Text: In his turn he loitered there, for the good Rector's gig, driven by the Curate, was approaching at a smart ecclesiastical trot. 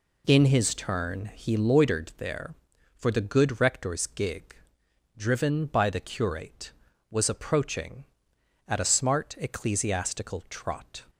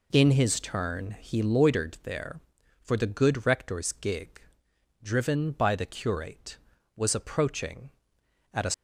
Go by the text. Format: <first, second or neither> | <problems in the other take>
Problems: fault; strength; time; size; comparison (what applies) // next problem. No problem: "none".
first | stops before "smart ecclesiastical trot"; at 8.7 s